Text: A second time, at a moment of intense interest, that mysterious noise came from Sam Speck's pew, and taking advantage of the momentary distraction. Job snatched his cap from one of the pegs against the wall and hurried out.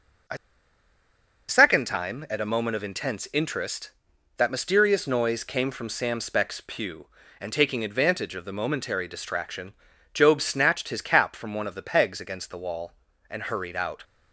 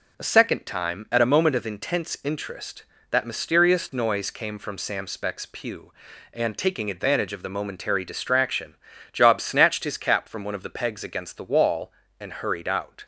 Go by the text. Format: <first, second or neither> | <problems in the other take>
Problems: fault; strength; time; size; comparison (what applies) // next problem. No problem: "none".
second | pauses between "A" and "second"; at 0.3 s; 1.1 s long